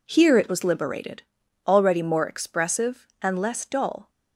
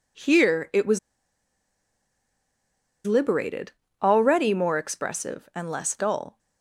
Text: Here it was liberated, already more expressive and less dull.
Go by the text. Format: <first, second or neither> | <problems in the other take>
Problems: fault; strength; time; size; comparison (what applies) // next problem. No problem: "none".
first | pauses between "was" and "liberated"; strong; at 0.9 s; 2.0 s long